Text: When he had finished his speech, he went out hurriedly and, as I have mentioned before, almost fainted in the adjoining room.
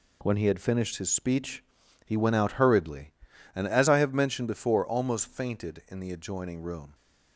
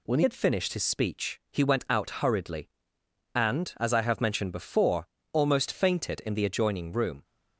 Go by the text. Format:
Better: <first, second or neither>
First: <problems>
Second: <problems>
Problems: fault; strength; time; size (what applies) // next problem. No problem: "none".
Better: first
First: none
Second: changes voice at "had"; from 0.2 s on; 7.0 s long